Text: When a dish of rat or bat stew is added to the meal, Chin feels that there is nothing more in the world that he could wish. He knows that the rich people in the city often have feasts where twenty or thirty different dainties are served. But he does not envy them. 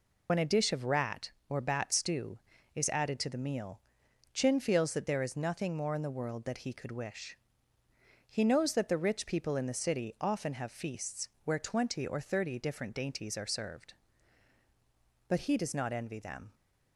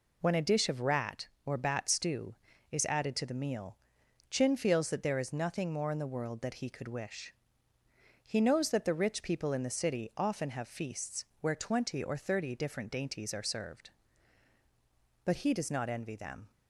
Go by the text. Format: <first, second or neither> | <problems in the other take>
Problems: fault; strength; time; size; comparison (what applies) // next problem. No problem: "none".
second | loses the start of "When"; at 0.2 s; 50 ms // pauses between "feasts" and "where"; slight; at 11.2 s; 0.16 s long; slight in the second